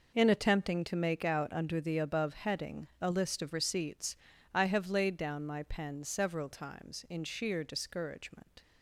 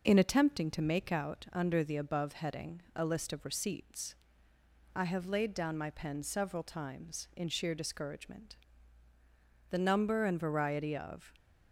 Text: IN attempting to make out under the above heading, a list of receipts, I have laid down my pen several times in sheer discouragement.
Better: first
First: none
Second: goes on to say "The number and variety of"; from 9.6 s on; 1.6 s long

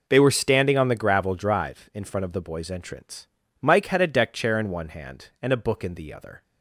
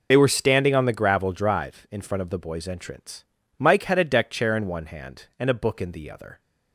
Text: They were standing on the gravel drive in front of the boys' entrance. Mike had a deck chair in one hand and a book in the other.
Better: first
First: none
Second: loses the start of "They"; at 0.1 s; 40 ms

